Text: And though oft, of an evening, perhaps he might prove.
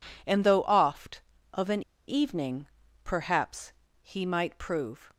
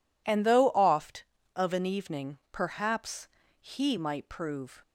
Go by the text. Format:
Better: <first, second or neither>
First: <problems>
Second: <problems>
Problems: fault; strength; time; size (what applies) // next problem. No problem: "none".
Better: second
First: pauses between "an" and "evening"; slight; at 1.8 s; 0.26 s long // pauses between "perhaps" and "he"; slight; at 3.7 s; 0.30 s long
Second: pauses between "perhaps" and "he"; slight; at 3.2 s; 0.32 s long